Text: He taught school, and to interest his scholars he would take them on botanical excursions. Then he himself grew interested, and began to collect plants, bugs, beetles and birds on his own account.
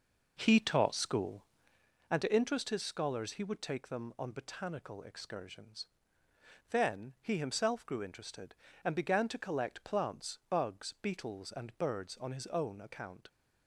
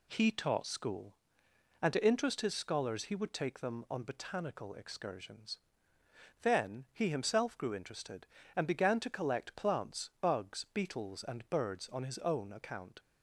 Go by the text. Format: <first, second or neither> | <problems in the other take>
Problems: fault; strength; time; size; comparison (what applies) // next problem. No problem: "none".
second | starts louder than the rest; noticeable; until 1.9 s; 5.5 dB